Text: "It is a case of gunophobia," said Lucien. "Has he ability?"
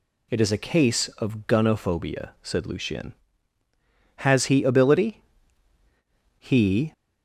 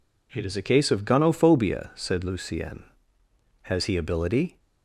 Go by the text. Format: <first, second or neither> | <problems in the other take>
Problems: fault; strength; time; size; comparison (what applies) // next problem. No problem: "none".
second | goes on to say "He"; from 6.3 s on; 0.54 s long